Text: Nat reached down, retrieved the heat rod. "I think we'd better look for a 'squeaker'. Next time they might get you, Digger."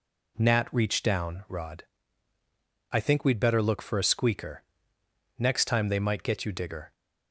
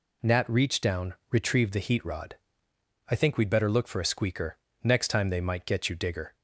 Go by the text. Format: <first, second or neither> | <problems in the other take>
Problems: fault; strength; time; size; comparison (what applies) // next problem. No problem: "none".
second | skips "retrieved the heat"; at 1.4 s